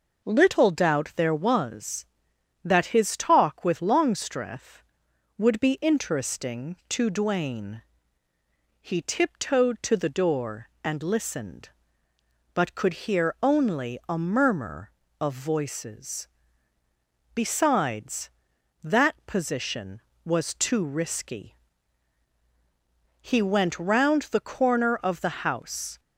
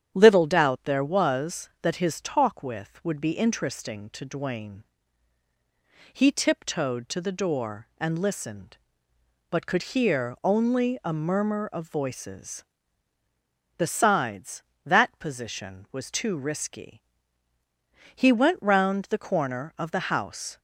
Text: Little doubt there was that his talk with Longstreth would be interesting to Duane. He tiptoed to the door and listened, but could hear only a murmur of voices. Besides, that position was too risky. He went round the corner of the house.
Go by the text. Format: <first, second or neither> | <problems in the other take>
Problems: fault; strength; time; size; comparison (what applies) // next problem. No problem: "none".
first | starts louder than the rest; strong; until 1.1 s; 9.5 dB // skips "Longstreth"; at 3.0 s